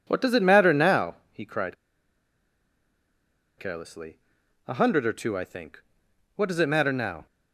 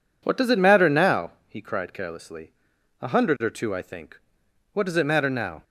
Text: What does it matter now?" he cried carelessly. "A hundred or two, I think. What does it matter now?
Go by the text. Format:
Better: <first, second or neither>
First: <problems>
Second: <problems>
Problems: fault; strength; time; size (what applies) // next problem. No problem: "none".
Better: second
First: pauses between "cried" and "carelessly"; strong; at 1.7 s; 1.8 s long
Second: none